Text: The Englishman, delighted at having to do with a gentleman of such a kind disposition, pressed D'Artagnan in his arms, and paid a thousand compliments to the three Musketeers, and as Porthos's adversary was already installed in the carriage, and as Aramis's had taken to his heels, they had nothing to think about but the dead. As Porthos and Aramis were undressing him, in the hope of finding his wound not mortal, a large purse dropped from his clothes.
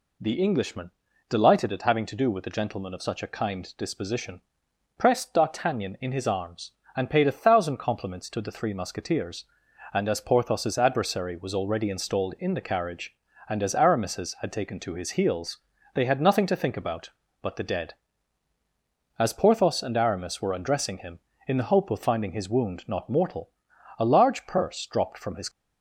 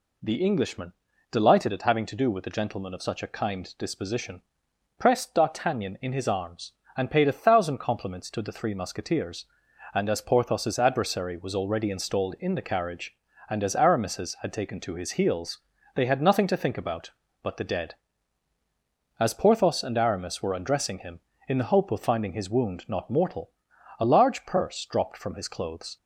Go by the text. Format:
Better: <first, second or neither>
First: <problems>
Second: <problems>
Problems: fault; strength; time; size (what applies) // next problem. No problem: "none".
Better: second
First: stops before "clothes"; at 25.4 s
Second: none